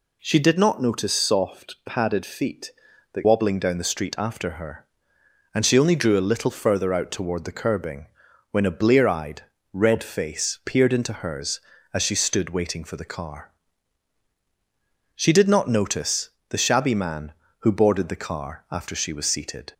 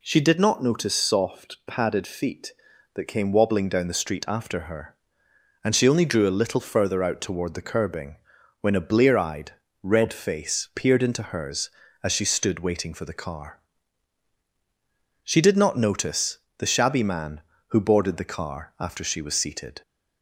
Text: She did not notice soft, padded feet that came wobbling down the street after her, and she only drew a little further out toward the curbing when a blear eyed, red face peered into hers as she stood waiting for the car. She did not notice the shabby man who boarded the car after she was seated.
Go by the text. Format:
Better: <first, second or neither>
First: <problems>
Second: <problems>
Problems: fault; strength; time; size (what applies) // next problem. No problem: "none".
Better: second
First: skips "came"; at 3.2 s // pauses between "curbing" and "when"; at 8.0 s; 0.44 s long // pauses between "notice" and "the"; slight; at 16.2 s; 0.20 s long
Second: pauses between "curbing" and "when"; at 8.1 s; 0.44 s long // pauses between "notice" and "the"; slight; at 16.3 s; 0.20 s long